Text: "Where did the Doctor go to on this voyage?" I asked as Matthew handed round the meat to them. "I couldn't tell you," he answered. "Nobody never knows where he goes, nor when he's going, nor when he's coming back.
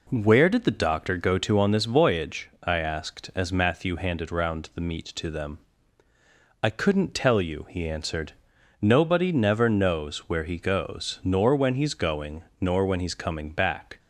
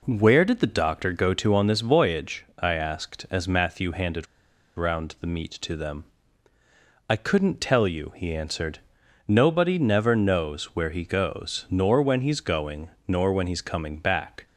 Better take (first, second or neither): first